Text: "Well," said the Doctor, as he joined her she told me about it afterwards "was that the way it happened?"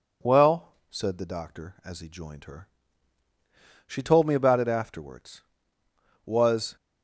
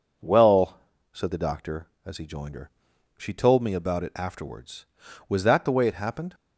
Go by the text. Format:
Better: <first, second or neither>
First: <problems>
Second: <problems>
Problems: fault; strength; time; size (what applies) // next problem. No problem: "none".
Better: second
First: pauses between "her" and "she"; at 2.6 s; 1.2 s long // stops before "that the way it happened"; at 6.7 s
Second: pauses between "her" and "she"; noticeable; at 2.7 s; 0.46 s long